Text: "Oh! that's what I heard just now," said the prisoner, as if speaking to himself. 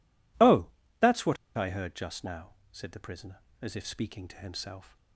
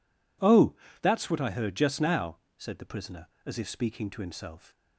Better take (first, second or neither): second